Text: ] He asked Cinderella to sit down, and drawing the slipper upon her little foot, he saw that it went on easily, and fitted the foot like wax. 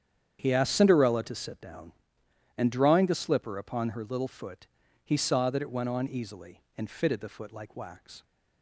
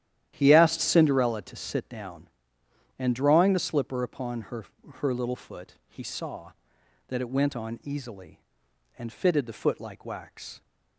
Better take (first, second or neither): first